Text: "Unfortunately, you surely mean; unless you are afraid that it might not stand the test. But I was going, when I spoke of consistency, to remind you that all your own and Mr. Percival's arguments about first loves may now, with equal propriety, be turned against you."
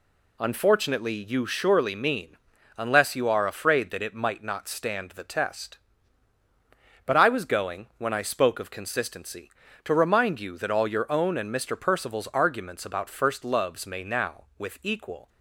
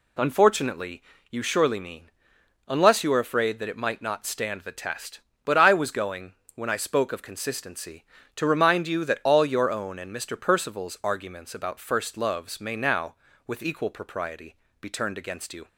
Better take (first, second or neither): second